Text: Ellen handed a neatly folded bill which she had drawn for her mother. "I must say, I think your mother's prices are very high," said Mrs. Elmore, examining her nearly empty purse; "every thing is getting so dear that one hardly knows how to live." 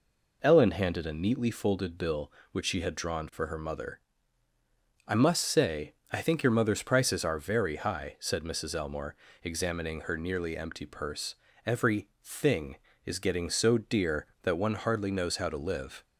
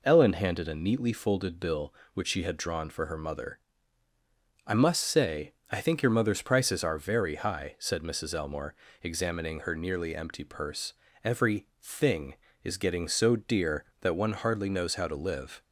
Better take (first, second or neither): neither